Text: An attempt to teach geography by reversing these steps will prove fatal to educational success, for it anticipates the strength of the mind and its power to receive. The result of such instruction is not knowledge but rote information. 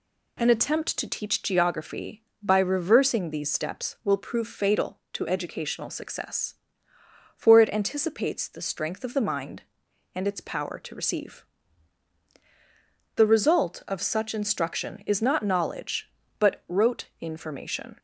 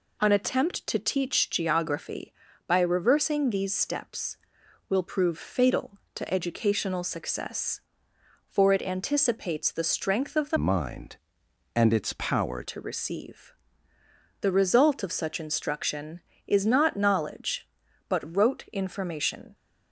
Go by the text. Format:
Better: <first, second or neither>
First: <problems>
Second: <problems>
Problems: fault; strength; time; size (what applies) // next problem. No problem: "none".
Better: first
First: none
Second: changes voice from "mind" to "power"; from 10.5 to 12.6 s; 2.1 s long